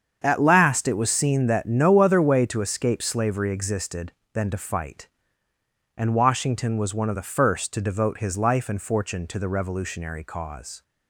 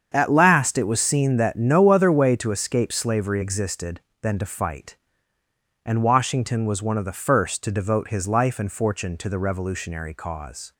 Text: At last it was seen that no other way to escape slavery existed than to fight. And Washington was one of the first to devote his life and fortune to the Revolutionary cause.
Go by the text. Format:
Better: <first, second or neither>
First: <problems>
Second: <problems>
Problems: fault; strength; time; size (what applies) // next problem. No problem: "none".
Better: neither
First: starts louder than the rest; strong; until 1.2 s; 7.5 dB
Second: starts louder than the rest; strong; until 1.1 s; 7.5 dB